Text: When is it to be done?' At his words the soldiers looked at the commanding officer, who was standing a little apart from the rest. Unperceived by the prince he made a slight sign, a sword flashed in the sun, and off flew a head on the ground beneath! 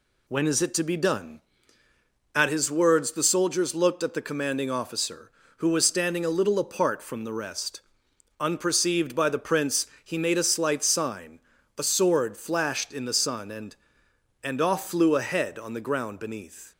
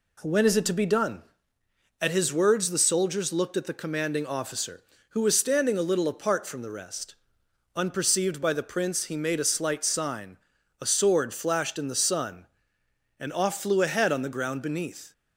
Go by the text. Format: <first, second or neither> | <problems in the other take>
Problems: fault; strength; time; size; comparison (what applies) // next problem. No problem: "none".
second | pauses between "prince" and "he"; slight; at 9.8 s; 0.16 s long // says "and" twice; at 14.4 s